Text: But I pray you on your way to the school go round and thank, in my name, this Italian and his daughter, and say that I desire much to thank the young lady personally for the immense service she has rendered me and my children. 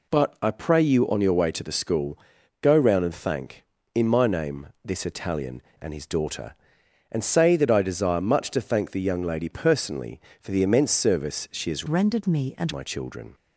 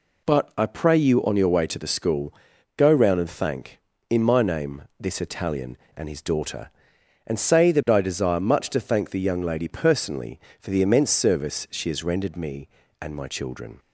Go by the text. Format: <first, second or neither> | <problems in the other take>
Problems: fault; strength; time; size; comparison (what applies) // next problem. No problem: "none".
second | pauses between "school" and "go"; at 2.1 s; 0.42 s long; also in the second // changes voice from "rendered" to "and"; from 11.8 to 12.7 s; 0.9 s long